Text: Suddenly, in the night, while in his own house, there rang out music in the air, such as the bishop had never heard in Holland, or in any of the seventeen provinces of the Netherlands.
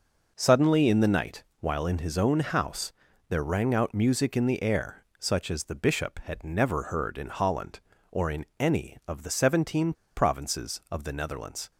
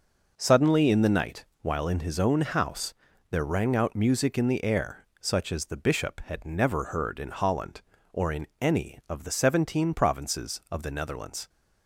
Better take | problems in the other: second | pauses between "in" and "any"; slight; at 8.4 s; 0.16 s long; slight in the second // pauses between "seventeen" and "provinces"; slight; at 9.9 s; 0.22 s long

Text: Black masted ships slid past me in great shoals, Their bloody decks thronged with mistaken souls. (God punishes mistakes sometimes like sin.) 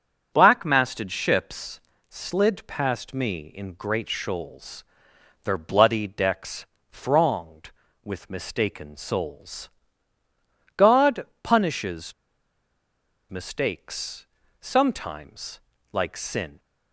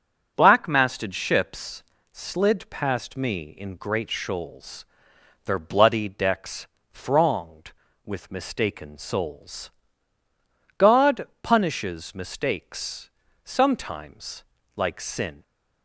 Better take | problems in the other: second | starts louder than the rest; until 1.3 s; 6.5 dB; also in the second // pauses between "ships" and "slid"; slight; at 1.7 s; 0.30 s long; slight in the second // pauses between "decks" and "thronged"; slight; at 6.6 s; 0.26 s long; slight in the second // pauses between "God" and "punishes"; slight; at 11.2 s; 0.16 s long // pauses between "punishes" and "mistakes"; at 12.1 s; 1.1 s long // pauses between "mistakes" and "sometimes"; slight; at 14.2 s; 0.34 s long; slight in the second // pauses between "sometimes" and "like"; slight; at 15.5 s; 0.32 s long; slight in the second

